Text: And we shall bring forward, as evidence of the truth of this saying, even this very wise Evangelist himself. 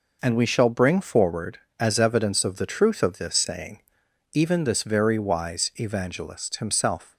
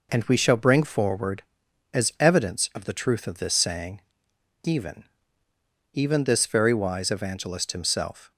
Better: first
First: none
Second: says "even" twice; at 5.9 s

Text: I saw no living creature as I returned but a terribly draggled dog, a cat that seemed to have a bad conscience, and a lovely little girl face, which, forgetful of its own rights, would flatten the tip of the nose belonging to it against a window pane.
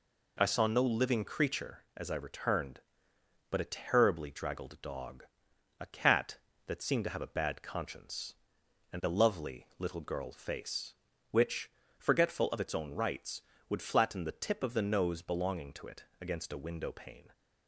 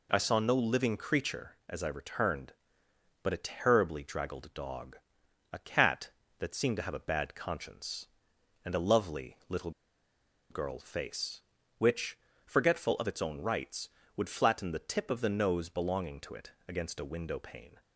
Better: first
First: pauses between "it" and "against"; slight; at 16.0 s; 0.16 s long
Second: pauses between "little" and "girl"; noticeable; at 9.7 s; 0.79 s long // pauses between "it" and "against"; slight; at 16.5 s; 0.16 s long

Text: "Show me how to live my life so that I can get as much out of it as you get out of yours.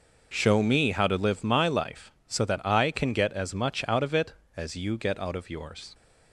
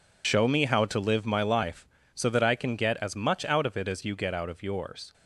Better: first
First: none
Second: loses the start of "Show"; at 0.2 s; 60 ms

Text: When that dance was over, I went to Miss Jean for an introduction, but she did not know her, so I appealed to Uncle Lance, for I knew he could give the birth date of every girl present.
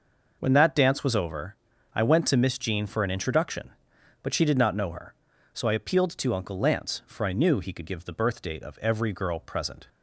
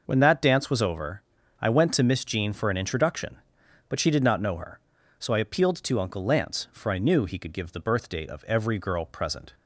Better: neither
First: none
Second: none

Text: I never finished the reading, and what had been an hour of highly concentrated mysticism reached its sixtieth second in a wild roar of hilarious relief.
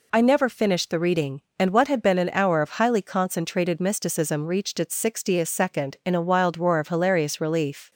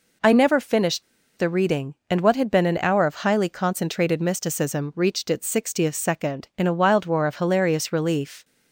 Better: first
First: none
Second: pauses between "finished" and "the"; slight; at 1.0 s; 0.35 s long

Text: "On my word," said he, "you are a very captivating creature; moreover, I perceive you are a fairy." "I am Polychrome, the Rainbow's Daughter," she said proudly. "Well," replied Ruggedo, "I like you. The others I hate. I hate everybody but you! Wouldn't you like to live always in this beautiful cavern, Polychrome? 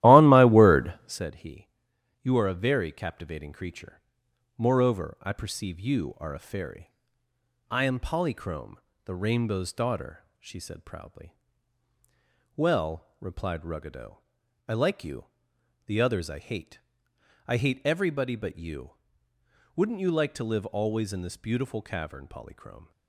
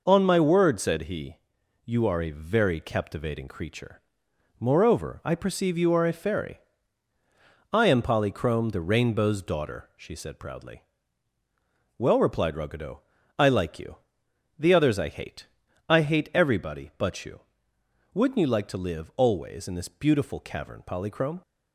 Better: second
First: starts louder than the rest; strong; until 1.2 s; 15 dB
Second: none

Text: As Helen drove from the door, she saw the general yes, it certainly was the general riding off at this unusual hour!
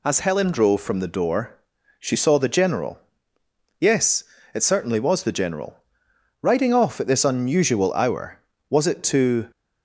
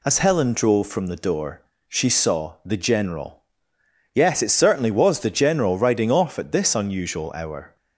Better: second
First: pauses between "general" and "yes"; noticeable; at 2.9 s; 0.80 s long // pauses between "general" and "riding"; noticeable; at 5.7 s; 0.66 s long // goes on to say "Was it to"; noticeable; from 8.7 s on; 0.80 s long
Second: pauses between "general" and "yes"; noticeable; at 3.3 s; 0.76 s long

